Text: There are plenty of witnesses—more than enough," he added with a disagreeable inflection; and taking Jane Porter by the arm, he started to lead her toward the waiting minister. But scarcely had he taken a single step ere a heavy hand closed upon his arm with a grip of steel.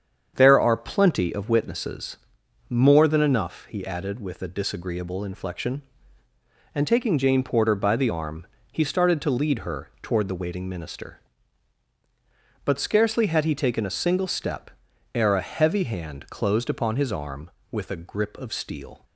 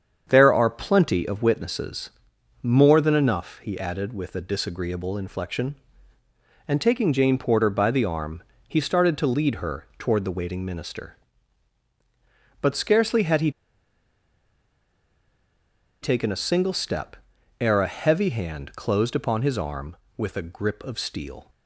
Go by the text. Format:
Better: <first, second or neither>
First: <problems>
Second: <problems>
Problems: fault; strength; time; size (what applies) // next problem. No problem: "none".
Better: first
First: starts louder than the rest; strong; until 1.3 s; 7.5 dB // pauses between "step" and "ere"; at 14.6 s; 0.44 s long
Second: starts louder than the rest; strong; until 1.3 s; 7.5 dB // pauses between "he" and "taken"; strong; at 13.4 s; 2.5 s long // pauses between "step" and "ere"; at 17.1 s; 0.44 s long